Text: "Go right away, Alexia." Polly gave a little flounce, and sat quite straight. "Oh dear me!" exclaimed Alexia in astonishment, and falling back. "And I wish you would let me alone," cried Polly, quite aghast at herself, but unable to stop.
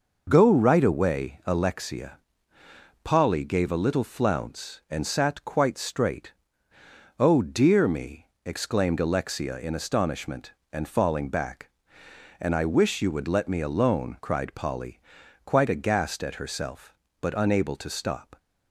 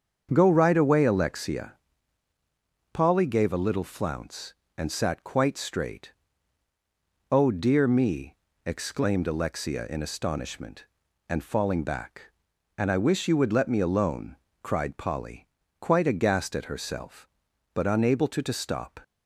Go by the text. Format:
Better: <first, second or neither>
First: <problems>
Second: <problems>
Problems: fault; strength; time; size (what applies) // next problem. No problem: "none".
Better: first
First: none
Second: starts louder than the rest; until 1.3 s; 7 dB // says "to" twice; at 18.4 s